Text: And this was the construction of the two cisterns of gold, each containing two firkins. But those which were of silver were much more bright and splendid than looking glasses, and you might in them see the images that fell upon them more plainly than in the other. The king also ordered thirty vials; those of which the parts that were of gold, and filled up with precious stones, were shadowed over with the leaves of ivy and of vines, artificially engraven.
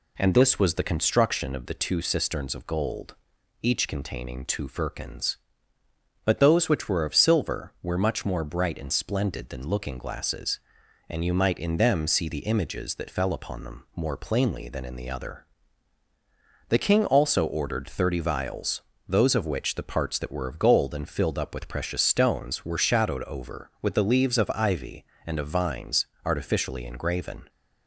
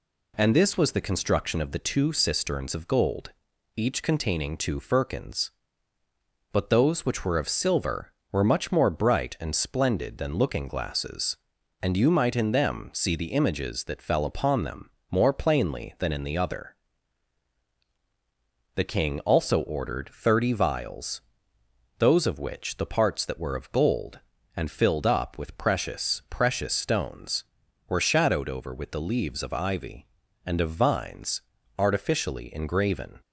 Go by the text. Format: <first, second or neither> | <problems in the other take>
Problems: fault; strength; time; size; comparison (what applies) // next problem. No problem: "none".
first | pauses between "them" and "more"; slight; at 14.9 s; 0.20 s long // says "precious" twice; at 26.2 s